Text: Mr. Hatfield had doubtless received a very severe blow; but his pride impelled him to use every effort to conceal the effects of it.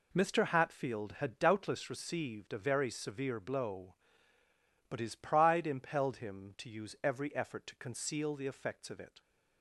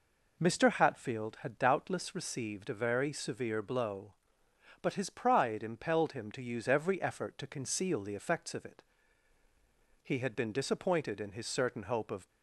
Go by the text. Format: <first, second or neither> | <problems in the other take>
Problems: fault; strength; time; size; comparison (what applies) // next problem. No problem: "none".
first | goes on to say "He had been disappointed in his certain hope of"; strong; from 10.0 s on; 2.2 s long